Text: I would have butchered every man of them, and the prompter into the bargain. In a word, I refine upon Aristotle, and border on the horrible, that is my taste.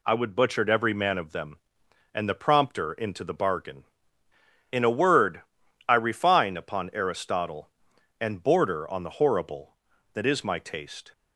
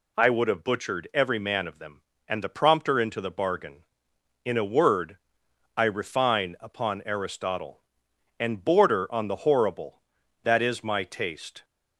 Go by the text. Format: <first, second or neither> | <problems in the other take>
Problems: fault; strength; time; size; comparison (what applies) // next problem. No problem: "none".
second | skips "have"; at 0.3 s